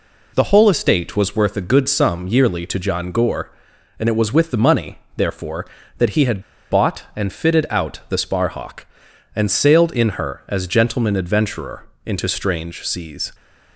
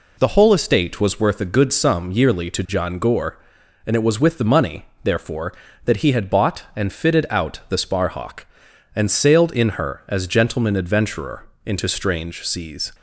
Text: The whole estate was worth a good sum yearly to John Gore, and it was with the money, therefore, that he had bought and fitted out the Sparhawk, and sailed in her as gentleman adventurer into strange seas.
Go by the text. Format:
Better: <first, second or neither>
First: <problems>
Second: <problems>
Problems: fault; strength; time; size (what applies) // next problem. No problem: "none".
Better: second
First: pauses between "had" and "bought"; slight; at 6.4 s; 0.27 s long // pauses between "adventurer" and "into"; slight; at 11.8 s; 0.18 s long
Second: pauses between "adventurer" and "into"; slight; at 11.4 s; 0.18 s long